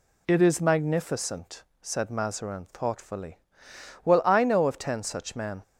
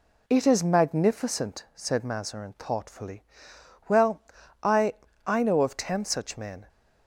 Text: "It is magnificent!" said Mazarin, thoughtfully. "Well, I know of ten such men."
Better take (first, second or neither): first